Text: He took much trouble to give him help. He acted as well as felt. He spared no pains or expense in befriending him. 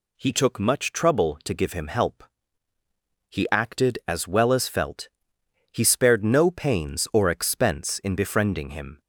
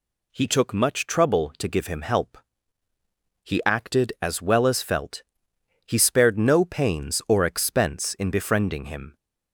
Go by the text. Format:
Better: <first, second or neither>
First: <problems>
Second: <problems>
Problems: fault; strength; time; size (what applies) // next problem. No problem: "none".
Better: neither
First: none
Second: none